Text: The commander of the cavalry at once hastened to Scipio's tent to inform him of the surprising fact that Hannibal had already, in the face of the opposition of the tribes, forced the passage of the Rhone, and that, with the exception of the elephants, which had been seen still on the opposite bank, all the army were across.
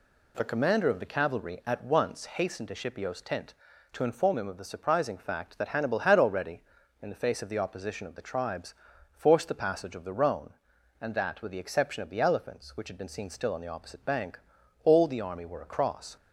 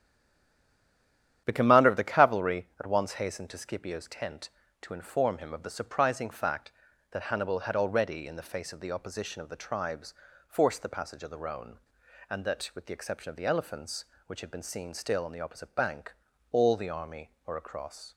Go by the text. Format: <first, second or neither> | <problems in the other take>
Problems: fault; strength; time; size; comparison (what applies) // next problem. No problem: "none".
first | stays silent before the first word; noticeable; until 1.4 s; 1.4 s long // starts louder than the rest; strong; until 2.4 s; 10 dB